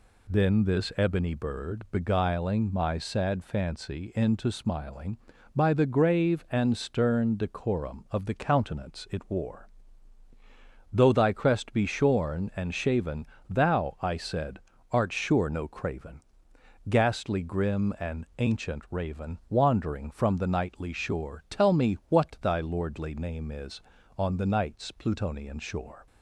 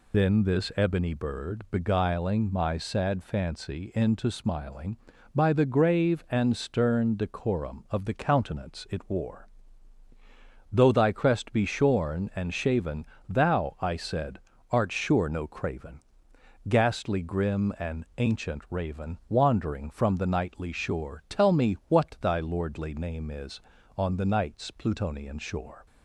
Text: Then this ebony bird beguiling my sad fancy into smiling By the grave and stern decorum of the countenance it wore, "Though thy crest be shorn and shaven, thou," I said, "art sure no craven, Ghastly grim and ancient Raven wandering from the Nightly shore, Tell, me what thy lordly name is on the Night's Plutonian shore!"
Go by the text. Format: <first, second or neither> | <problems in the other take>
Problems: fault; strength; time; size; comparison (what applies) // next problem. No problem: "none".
first | loses the start of "Then"; at 0.1 s; 80 ms